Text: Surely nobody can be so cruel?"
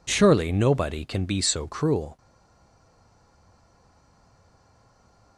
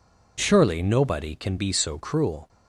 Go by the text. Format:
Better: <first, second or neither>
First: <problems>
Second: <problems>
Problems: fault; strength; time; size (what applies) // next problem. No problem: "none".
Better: second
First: stays silent after the last word; strong; from 2.1 s on; 3.2 s long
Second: none